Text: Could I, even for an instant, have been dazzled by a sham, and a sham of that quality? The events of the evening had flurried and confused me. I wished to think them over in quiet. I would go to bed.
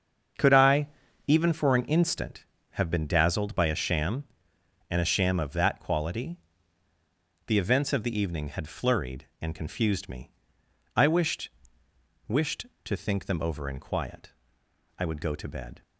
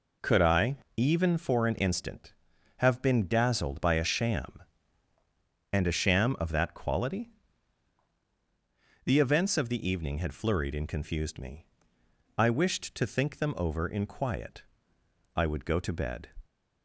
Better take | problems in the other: second | starts louder than the rest; strong; until 1.8 s; 7 dB // says "wished" twice; at 12.2 s

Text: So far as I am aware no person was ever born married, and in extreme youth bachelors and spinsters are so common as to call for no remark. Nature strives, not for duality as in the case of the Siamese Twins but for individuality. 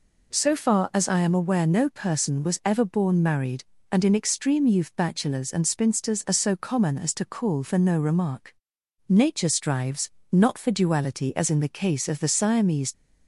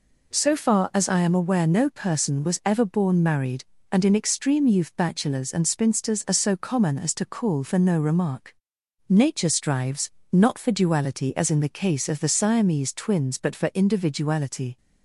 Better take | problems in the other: second | stops before "Twins but for individuality"; at 12.9 s

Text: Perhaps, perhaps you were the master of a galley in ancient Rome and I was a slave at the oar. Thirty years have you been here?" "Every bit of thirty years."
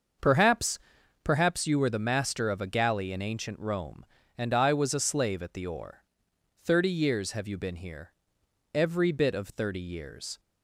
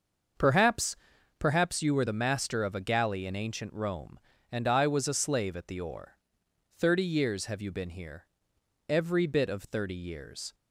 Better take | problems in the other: neither | starts louder than the rest; the same in both

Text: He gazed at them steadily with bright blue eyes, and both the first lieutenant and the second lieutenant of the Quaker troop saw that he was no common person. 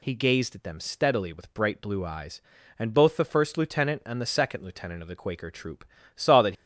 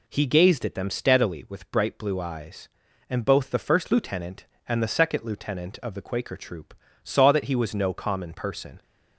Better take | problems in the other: second | pauses between "troop" and "saw"; slight; at 5.8 s; 0.28 s long; slight in the second // stops before "he was no common person"; at 6.5 s

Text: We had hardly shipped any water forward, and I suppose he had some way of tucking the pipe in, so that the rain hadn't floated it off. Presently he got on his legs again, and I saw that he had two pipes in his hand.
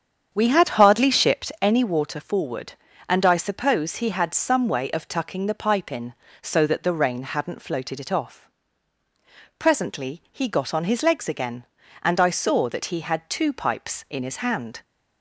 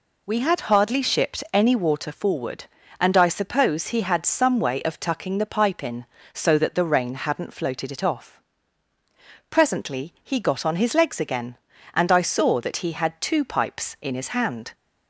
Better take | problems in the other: second | starts louder than the rest; strong; until 1.5 s; 8 dB

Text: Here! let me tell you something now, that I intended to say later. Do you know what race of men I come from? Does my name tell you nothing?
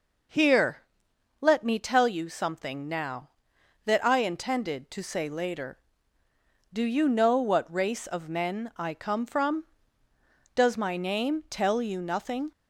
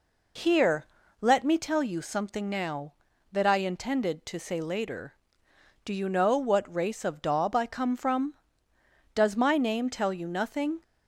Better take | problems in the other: first | says "daub" for "men"; at 7.2 s

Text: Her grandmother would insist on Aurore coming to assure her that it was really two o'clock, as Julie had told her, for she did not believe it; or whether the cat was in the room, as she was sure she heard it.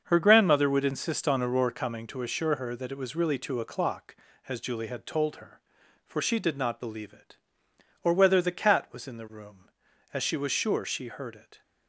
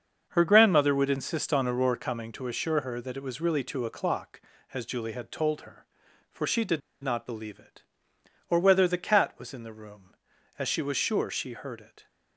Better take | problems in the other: first | starts louder than the rest; until 1.3 s; 6.5 dB; also in the first // pauses between "did" and "not"; slight; at 6.8 s; 0.22 s long

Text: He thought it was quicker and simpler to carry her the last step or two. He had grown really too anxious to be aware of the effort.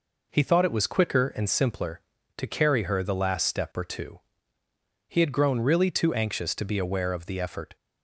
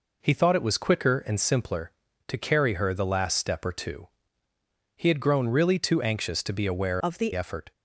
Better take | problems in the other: first | changes voice from "of" to "the"; from 7.0 to 7.3 s; 0.3 s long

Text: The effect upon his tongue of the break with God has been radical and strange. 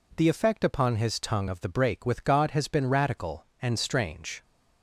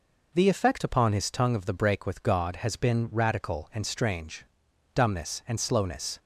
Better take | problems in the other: first | goes on to say "Dumbness and slowness"; noticeable; from 4.9 s on; 1.2 s long

